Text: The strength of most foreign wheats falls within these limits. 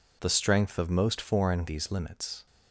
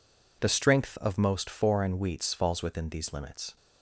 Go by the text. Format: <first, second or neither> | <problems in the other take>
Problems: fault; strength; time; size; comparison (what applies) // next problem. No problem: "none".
second | skips "wheats falls within"; at 1.6 s